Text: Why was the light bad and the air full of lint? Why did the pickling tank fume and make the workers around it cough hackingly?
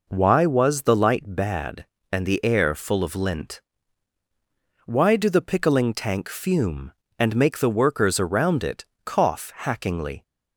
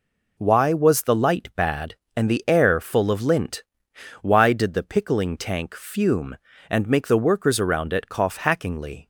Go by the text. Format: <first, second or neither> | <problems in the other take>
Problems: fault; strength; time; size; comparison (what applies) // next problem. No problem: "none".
second | says "do" for "did"; at 5.1 s // pauses between "it" and "cough"; slight; at 8.8 s; 0.18 s long